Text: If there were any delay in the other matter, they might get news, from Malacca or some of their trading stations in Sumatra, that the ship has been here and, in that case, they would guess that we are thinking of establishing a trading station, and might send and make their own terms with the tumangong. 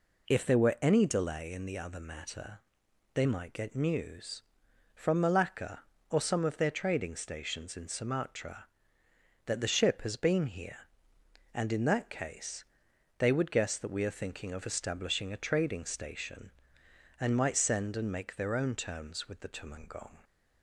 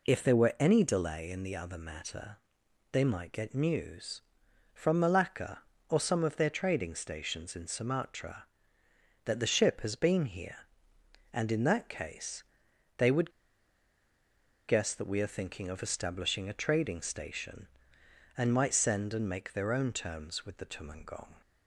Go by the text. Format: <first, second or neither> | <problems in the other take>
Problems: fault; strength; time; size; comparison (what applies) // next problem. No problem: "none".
first | pauses between "would" and "guess"; strong; at 13.2 s; 1.3 s long